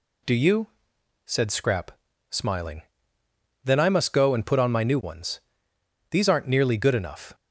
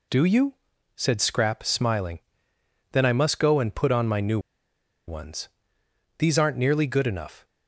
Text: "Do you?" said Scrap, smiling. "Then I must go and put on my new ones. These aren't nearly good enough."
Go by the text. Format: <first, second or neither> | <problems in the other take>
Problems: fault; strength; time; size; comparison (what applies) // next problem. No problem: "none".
first | pauses between "new" and "ones"; noticeable; at 4.3 s; 0.69 s long